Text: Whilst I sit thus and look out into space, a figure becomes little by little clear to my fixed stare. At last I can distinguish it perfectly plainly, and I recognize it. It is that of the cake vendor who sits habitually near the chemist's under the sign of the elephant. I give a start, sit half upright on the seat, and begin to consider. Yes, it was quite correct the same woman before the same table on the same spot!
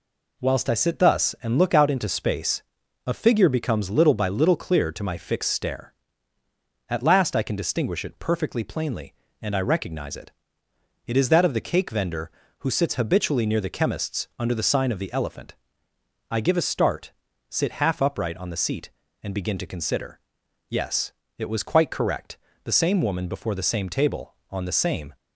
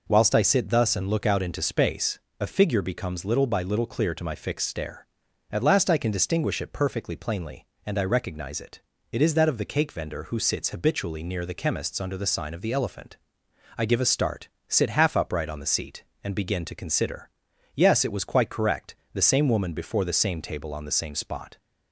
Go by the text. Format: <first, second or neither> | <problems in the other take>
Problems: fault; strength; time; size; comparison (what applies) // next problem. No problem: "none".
second | pauses between "correct" and "the"; slight; at 22.3 s; 0.26 s long; slight in the second // stops before "spot"; at 25.1 s